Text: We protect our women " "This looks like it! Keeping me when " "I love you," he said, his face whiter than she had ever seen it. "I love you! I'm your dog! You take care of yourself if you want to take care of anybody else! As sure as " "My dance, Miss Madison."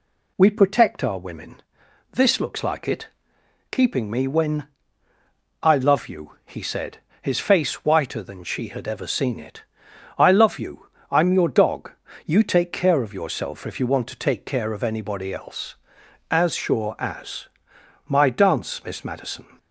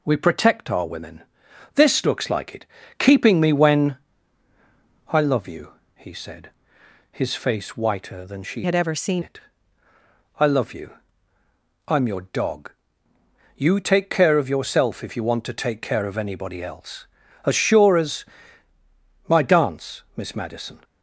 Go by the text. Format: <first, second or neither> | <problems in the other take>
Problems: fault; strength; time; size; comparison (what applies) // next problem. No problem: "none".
first | changes voice from "had" to "seen"; from 8.6 to 9.2 s; 0.6 s long